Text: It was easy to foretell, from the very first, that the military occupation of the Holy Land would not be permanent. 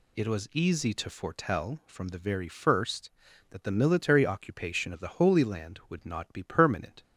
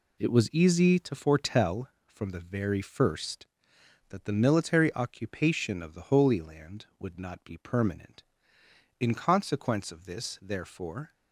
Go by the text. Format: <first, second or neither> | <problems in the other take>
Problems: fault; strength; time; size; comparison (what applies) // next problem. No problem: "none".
first | goes on to say "In consequence of this therefore"; strong; from 8.9 s on; 2.1 s long